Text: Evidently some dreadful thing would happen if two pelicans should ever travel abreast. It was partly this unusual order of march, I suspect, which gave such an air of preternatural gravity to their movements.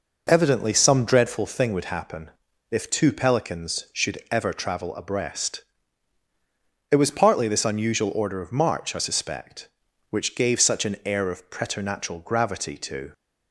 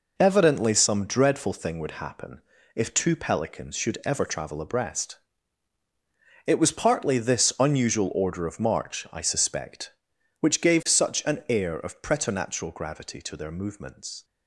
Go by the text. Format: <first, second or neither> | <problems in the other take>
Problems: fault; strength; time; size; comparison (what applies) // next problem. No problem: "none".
second | pauses between "happen" and "if"; at 2.2 s; 0.40 s long; slight in the second // stops before "their movements"; at 13.1 s